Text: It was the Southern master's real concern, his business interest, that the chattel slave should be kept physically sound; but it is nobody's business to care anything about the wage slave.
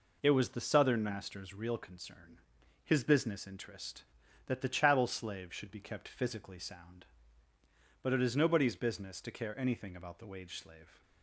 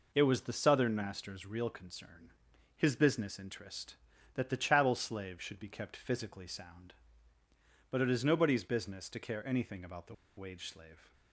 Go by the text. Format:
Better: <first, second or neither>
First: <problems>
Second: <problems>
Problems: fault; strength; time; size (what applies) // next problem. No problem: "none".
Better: first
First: none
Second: pauses between "the" and "wage"; slight; at 10.1 s; 0.23 s long